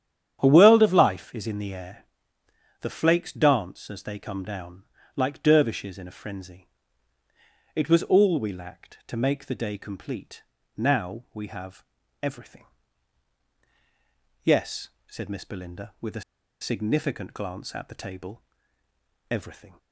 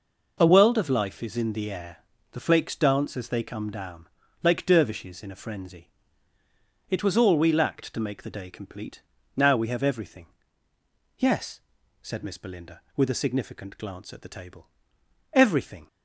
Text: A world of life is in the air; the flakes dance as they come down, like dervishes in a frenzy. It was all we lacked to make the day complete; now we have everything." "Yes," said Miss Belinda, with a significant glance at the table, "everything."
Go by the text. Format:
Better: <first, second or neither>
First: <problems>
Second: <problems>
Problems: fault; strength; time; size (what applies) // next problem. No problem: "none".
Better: second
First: starts louder than the rest; strong; until 1.4 s; 9.5 dB // pauses between "have" and "everything"; at 11.8 s; 0.38 s long // pauses between "a" and "significant"; at 16.2 s; 0.40 s long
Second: none